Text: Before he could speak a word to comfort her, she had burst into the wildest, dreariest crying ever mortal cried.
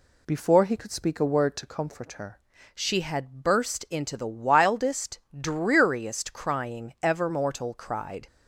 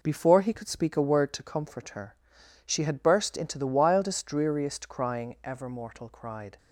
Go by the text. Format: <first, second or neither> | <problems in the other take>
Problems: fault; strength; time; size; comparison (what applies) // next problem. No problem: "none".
second | changes voice at "she"; from 2.7 s on; 5.5 s long